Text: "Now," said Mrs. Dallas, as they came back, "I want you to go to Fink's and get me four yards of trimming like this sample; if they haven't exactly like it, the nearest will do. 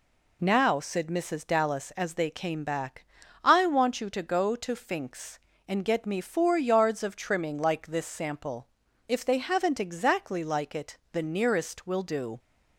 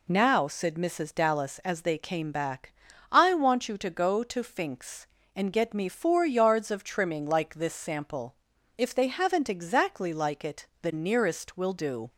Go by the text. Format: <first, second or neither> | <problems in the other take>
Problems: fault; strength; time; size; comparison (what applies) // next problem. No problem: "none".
neither | none